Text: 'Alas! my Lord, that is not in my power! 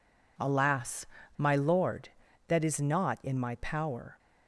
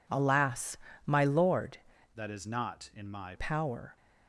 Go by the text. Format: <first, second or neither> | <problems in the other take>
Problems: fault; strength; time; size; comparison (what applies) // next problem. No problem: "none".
first | changes voice from "that" to "my"; from 2.1 to 3.3 s; 1.2 s long